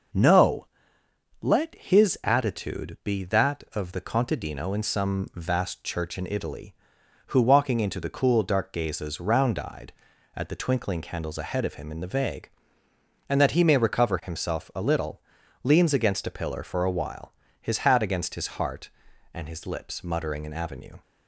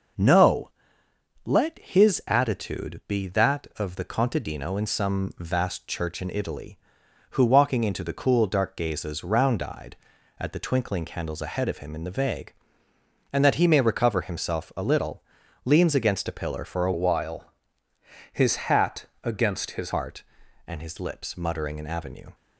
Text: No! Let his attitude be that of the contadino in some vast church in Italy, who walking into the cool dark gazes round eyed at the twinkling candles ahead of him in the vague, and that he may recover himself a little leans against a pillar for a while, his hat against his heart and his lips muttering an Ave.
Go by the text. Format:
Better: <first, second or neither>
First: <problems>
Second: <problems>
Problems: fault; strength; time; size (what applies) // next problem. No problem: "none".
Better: first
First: pauses between "little" and "leans"; at 15.2 s; 0.42 s long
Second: pauses between "little" and "leans"; at 15.2 s; 0.42 s long // changes voice from "while" to "his"; from 16.9 to 19.9 s; 3.0 s long // pauses between "hat" and "against"; slight; at 19.0 s; 0.18 s long